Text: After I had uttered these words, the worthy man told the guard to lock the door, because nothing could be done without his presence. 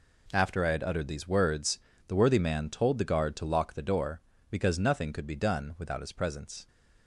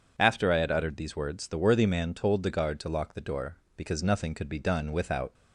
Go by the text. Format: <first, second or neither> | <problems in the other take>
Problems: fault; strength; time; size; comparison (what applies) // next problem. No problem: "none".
first | stops before "his presence"; at 5.3 s